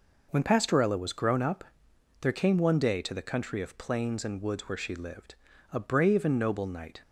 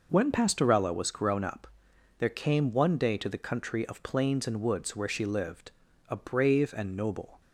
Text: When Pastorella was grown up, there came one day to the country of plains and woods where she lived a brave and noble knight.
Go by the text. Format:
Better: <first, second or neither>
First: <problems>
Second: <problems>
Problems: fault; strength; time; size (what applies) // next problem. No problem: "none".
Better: first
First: pauses between "lived" and "a"; at 5.3 s; 0.38 s long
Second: pauses between "lived" and "a"; at 5.7 s; 0.38 s long // stops before "knight"; at 7.4 s